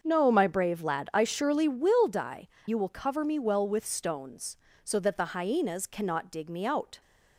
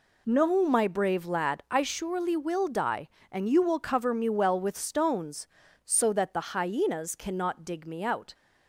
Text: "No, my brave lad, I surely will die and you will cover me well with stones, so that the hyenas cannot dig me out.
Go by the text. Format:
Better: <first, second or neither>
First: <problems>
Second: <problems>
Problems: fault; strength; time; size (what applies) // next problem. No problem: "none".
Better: second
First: starts louder than the rest; until 1.0 s; 6.5 dB // skips "and"; at 2.5 s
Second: none